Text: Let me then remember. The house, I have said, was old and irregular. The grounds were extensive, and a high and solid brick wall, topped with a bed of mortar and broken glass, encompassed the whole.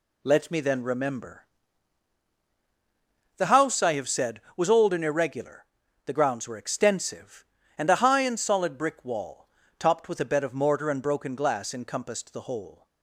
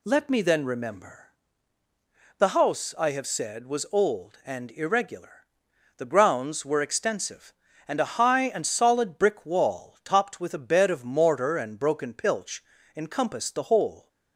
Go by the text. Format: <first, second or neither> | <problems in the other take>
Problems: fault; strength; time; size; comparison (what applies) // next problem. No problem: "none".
first | says "pilch" for "glass"; at 12.1 s